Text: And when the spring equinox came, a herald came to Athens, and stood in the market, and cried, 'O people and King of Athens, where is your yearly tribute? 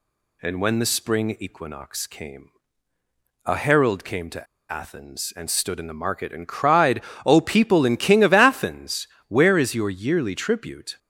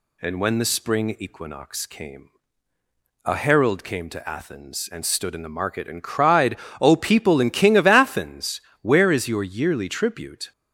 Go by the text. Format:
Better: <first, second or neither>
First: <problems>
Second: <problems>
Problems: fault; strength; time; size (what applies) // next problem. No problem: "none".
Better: second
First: pauses between "to" and "Athens"; slight; at 4.4 s; 0.26 s long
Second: none